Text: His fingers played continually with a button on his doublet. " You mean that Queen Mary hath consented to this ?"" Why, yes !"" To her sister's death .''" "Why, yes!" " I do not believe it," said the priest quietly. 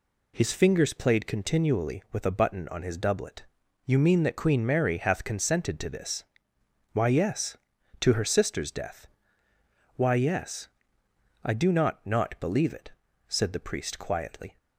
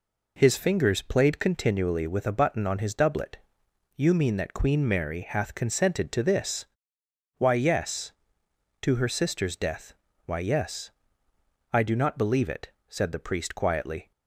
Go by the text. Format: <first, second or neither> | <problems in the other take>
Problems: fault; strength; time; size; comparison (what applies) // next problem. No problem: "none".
second | says "not" twice; at 12.0 s